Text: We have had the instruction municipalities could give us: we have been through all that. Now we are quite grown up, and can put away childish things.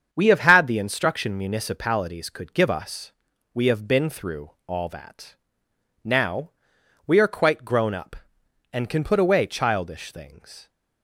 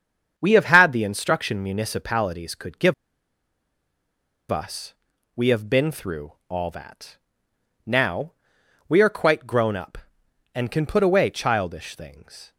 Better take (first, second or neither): first